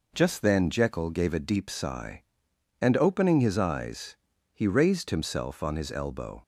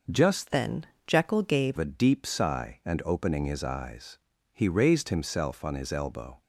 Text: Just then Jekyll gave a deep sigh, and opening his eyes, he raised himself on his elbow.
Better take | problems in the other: first | changes voice from "then" to "gave"; from 0.5 to 1.7 s; 1.2 s long // pauses between "then" and "Jekyll"; slight; at 0.8 s; 0.20 s long

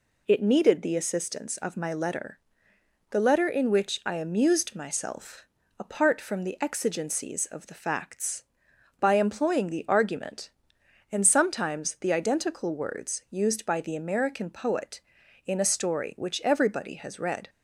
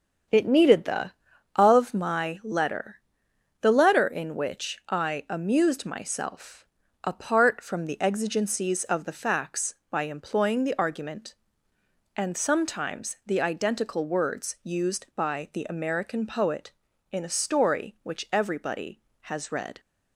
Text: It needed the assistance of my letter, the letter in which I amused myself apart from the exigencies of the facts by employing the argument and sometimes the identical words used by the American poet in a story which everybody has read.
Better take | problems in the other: first | starts louder than the rest; strong; until 1.7 s; 7 dB // skips "assistance"; at 1.3 s // pauses between "myself" and "apart"; slight; at 6.6 s; 0.36 s long; slight in the first

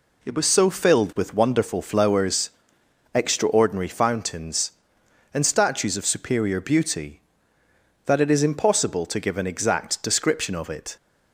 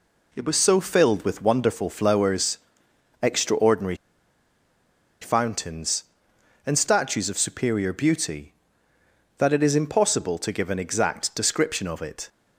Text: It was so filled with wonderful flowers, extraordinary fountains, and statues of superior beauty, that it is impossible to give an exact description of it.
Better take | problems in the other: first | pauses between "extraordinary" and "fountains"; strong; at 3.9 s; 1.2 s long

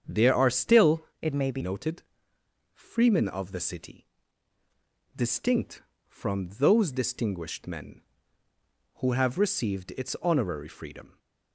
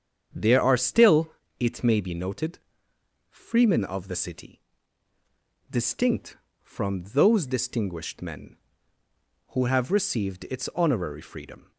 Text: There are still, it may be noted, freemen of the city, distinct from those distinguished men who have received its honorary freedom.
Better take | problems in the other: second | starts louder than the rest; strong; until 1.2 s; 7.5 dB; strong in the second // changes voice from "it" to "be"; from 1.2 to 1.6 s; 0.4 s long

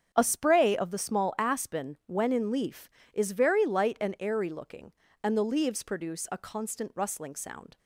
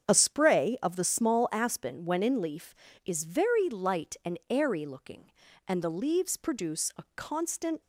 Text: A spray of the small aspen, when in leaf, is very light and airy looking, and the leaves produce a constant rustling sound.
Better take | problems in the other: first | starts louder than the rest; strong; until 1.1 s; 8 dB; strong in the first // stops before "rustling sound"; at 7.8 s

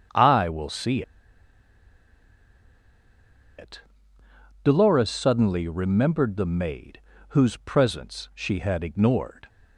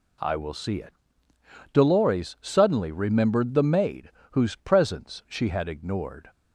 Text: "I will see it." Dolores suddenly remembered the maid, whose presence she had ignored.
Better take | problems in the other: second | starts louder than the rest; strong; until 3.7 s; 7.5 dB // pauses between "see" and "it"; strong; at 1.0 s; 2.5 s long

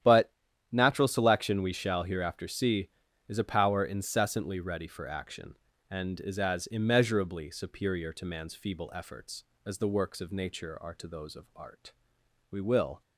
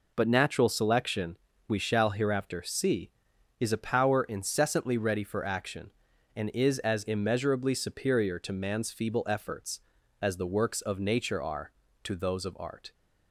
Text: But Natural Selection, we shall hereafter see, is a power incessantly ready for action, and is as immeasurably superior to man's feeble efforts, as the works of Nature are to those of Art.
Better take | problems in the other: second | starts louder than the rest; strong; until 1.4 s; 10.5 dB // pauses between "But" and "Natural"; at 0.3 s; 0.40 s long // goes on to say "We will"; from 12.4 s on; 0.52 s long

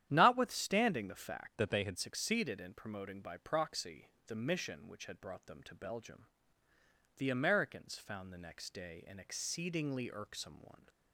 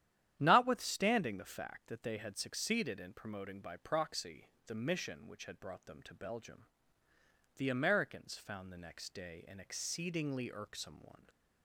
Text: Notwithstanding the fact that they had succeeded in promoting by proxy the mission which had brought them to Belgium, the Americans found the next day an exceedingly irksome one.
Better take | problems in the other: second | starts louder than the rest; strong; until 1.1 s; 10.5 dB; strong in the second // changes voice from "that" to "had"; from 1.5 to 1.9 s; 0.4 s long // pauses between "proxy" and "the"; slight; at 4.0 s; 0.18 s long; slight in the second

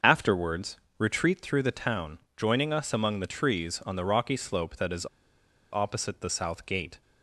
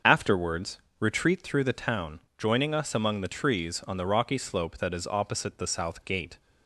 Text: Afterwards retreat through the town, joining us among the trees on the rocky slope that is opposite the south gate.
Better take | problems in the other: second | starts louder than the rest; until 1.2 s; 6.5 dB; also in the second // pauses between "Afterwards" and "retreat"; slight; at 0.7 s; 0.22 s long; slight in the second // pauses between "is" and "opposite"; noticeable; at 5.0 s; 0.65 s long

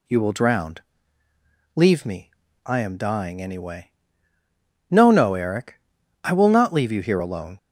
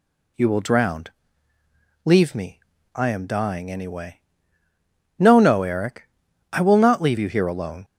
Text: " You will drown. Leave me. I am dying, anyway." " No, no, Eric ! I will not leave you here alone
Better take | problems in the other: neither | none

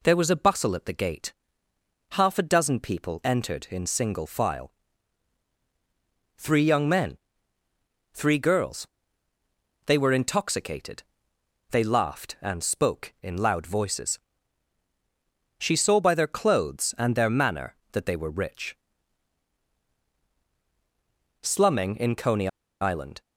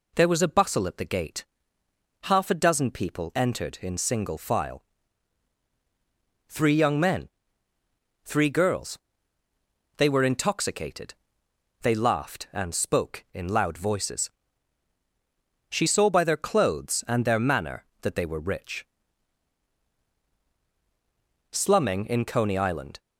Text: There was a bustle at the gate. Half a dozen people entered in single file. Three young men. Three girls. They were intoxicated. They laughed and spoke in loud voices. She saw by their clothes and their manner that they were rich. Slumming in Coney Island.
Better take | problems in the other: second | pauses between "Coney" and "Island"; slight; at 22.4 s; 0.33 s long

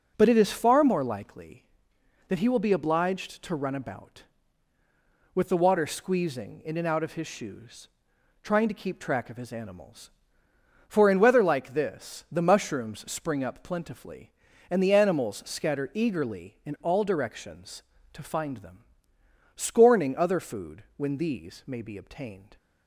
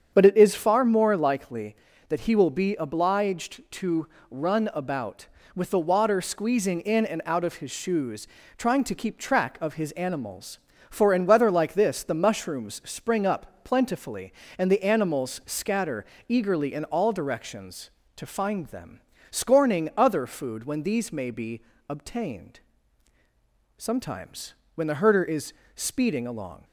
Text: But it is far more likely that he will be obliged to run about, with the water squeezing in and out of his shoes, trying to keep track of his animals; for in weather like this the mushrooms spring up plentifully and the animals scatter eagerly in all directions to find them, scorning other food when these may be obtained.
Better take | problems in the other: first | starts louder than the rest; strong; until 1.1 s; 7.5 dB // pauses between "to" and "run"; slight; at 4.0 s; 0.24 s long // pauses between "scatter" and "eagerly"; slight; at 16.0 s; 0.24 s long // pauses between "be" and "obtained"; slight; at 21.6 s; 0.26 s long // goes on to say "Sometimes when the herder is speeding along"; strong; from 23.7 s on; 2.8 s long

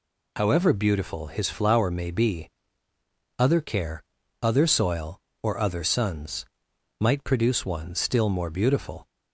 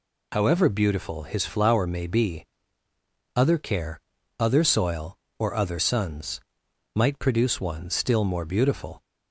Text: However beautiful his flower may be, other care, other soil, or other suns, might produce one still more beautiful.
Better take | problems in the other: neither | none

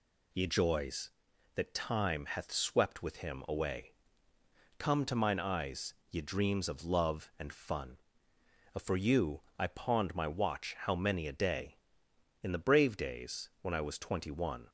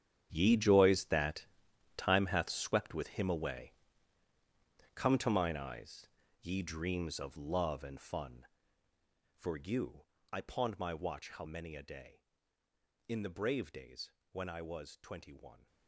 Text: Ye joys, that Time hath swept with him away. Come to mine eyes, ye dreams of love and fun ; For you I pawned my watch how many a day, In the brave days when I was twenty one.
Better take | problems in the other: first | gets quieter; strong; throughout; 16 dB // pauses between "that" and "Time"; noticeable; at 1.4 s; 0.52 s long // pauses between "you" and "I"; slight; at 10.0 s; 0.26 s long; slight in the first // pauses between "days" and "when"; slight; at 14.1 s; 0.18 s long

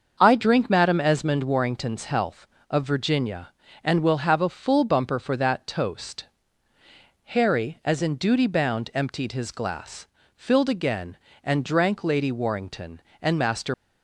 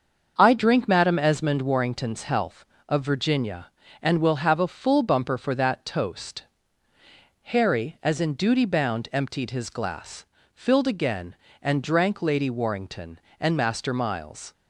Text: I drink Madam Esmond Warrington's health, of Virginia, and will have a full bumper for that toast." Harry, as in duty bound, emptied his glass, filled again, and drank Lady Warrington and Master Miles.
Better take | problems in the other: second | starts louder than the rest; until 1.2 s; 6.5 dB; also in the second // stops before "Miles"; at 13.7 s

